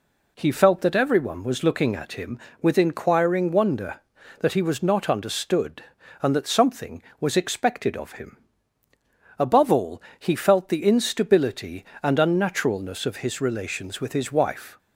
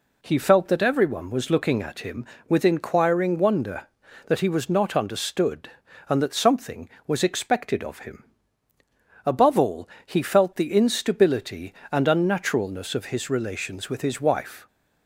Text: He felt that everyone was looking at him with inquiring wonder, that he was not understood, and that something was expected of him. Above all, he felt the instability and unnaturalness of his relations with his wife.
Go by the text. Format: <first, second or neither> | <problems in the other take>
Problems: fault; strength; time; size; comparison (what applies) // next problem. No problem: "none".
neither | none